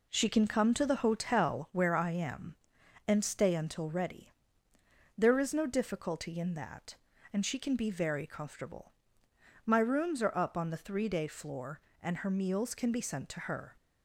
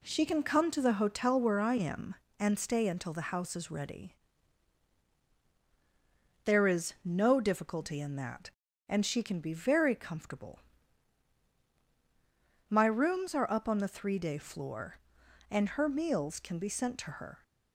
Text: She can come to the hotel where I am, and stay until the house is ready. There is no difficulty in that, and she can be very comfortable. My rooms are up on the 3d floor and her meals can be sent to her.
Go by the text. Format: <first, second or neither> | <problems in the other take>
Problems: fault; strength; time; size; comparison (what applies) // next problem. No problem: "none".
second | skips "the house is"; at 3.8 s